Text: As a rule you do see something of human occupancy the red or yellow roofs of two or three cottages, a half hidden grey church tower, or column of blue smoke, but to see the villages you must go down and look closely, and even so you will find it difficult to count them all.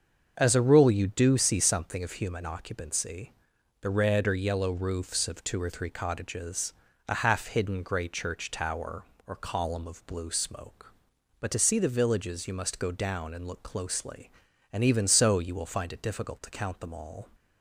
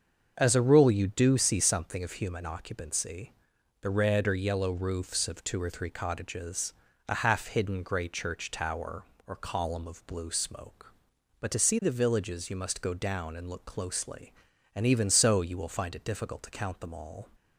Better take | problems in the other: neither | starts louder than the rest; the same in both // pauses between "occupancy" and "the"; noticeable; the same in both

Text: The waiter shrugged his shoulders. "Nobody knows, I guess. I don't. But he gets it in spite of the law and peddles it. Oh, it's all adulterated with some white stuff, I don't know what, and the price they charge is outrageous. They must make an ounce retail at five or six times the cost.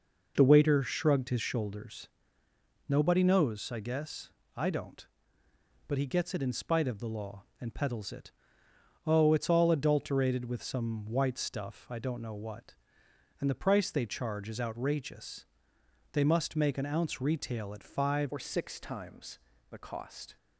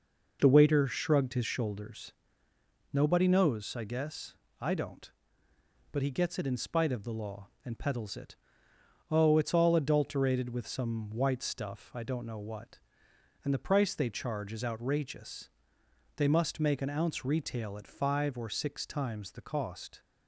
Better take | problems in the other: second | changes voice at "or"; from 18.3 s on; 2.0 s long // pauses between "times" and "the"; slight; at 19.3 s; 0.32 s long

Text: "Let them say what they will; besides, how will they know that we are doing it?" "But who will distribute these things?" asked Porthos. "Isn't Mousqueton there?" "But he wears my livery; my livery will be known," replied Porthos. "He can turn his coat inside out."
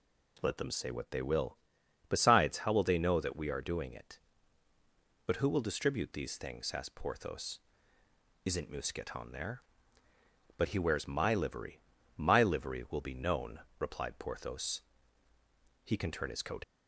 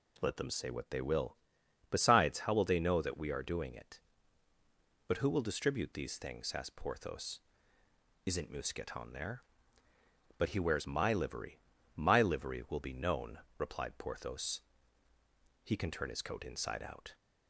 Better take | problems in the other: second | stops before "inside out"; at 16.6 s

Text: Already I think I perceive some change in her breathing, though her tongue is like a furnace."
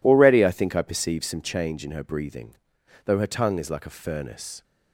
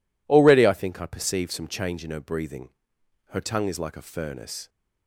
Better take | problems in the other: first | skips "though"; at 2.9 s

